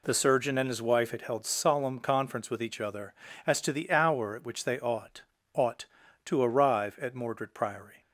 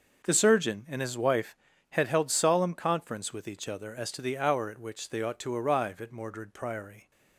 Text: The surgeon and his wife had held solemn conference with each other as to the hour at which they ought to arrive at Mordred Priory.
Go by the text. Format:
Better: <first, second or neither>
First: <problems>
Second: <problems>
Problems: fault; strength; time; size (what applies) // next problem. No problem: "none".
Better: second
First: says "ought" twice; at 5.5 s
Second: none